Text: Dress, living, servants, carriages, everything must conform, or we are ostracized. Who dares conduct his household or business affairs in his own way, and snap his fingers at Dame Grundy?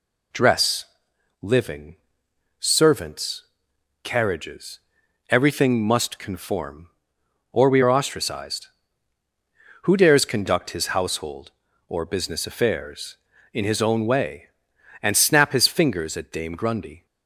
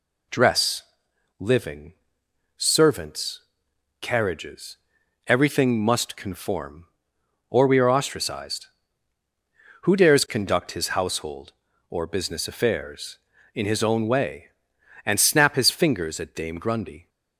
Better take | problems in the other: neither | none

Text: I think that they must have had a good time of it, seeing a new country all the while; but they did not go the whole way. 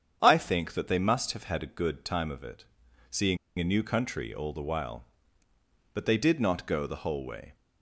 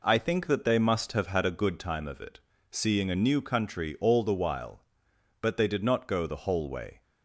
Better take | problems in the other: second | starts louder than the rest; strong; until 1.2 s; 8 dB // pauses between "seeing" and "a"; slight; at 3.3 s; 0.22 s long

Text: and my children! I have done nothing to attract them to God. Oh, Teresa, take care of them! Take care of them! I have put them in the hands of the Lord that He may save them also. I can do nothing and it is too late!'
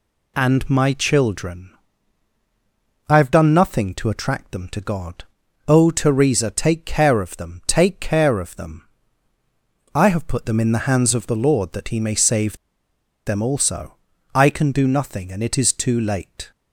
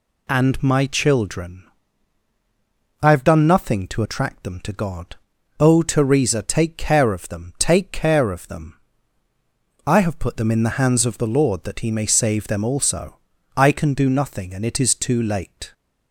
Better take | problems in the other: second | pauses between "save" and "them"; noticeable; at 12.5 s; 0.70 s long

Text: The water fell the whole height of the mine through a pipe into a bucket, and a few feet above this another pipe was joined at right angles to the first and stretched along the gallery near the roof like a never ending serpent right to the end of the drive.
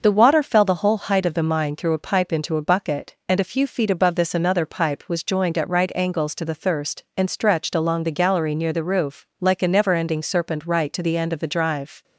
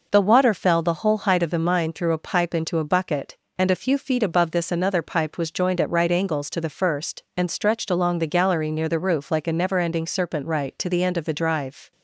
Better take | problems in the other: second | starts louder than the rest; noticeable; until 1.0 s; 6 dB // says "thirst" for "first"; at 6.5 s

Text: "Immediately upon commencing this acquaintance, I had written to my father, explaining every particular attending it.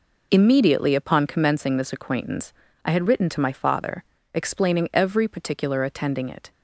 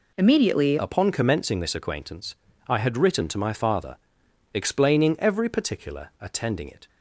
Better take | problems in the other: first | changes voice at "upon"; from 0.7 s on; 6.1 s long

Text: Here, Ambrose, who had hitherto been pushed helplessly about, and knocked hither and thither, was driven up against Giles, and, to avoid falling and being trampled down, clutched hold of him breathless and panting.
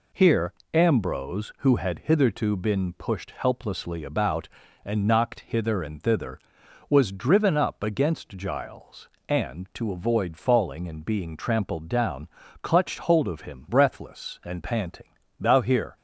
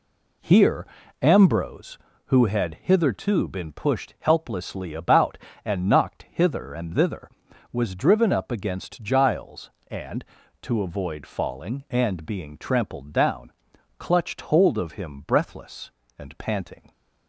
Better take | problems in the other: second | goes on to say "Thou here"; from 15.3 s on; 0.56 s long

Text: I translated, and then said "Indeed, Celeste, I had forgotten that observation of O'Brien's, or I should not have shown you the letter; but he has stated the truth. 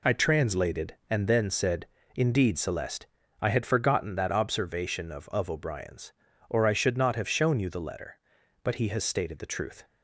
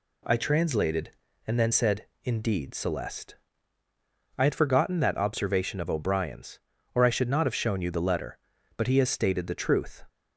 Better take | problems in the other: second | pauses between "said" and "Indeed"; slight; at 1.8 s; 0.31 s long; slight in the second // says "of" twice; at 5.2 s

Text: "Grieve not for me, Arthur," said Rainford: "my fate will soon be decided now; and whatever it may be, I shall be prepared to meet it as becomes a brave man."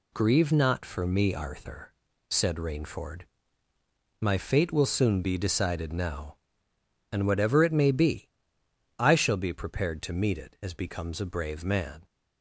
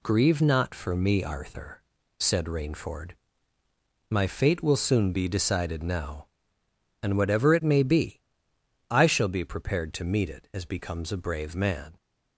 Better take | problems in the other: neither | none

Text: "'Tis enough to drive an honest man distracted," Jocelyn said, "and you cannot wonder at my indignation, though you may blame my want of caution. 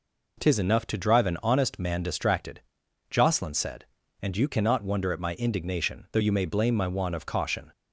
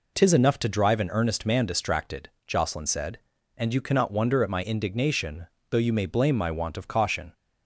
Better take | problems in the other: first | says "earnest" for "honest"; at 1.0 s

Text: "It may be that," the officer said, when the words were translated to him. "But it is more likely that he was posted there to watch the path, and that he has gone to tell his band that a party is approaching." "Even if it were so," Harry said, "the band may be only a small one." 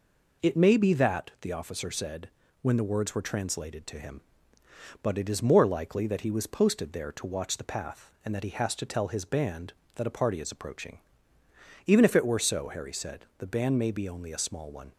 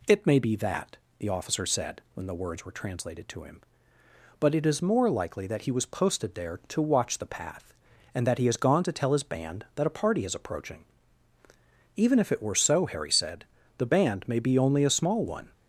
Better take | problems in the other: second | skips "gone"; at 8.7 s

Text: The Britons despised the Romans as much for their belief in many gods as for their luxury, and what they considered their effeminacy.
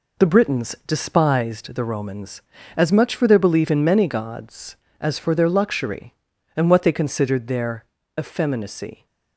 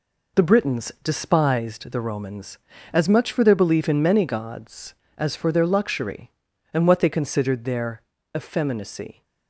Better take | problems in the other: neither | pauses between "their" and "effeminacy"; slight; the same in both

